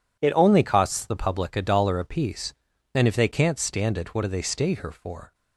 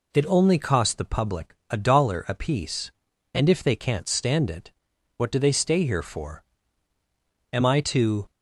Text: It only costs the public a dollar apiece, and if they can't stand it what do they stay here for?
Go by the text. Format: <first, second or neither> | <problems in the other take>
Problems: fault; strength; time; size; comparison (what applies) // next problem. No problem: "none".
first | pauses between "it" and "what"; at 4.7 s; 0.44 s long // goes on to say "Am I to"; noticeable; from 7.5 s on; 0.77 s long